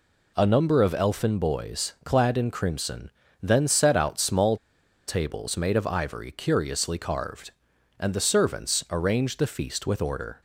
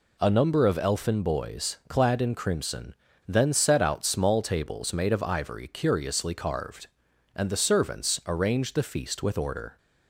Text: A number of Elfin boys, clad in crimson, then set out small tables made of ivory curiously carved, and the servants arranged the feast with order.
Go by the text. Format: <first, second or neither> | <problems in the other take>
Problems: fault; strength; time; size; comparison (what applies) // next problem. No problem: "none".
second | pauses between "small" and "tables"; noticeable; at 4.5 s; 0.51 s long